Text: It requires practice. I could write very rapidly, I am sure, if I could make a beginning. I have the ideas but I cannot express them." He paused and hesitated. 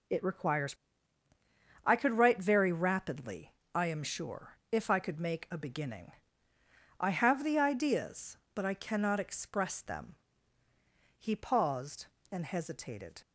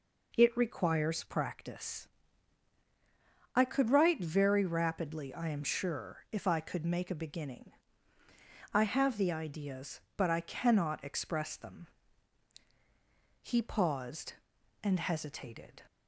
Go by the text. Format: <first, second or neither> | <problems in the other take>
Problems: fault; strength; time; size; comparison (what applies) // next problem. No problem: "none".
second | skips "practice"; at 1.2 s